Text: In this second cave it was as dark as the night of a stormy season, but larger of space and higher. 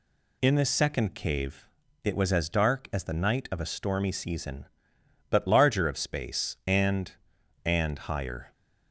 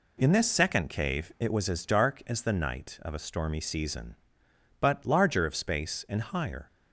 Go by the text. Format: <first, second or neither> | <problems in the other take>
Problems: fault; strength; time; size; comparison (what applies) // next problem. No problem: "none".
second | pauses between "cave" and "it"; at 1.6 s; 0.38 s long // says "and" twice; at 7.6 s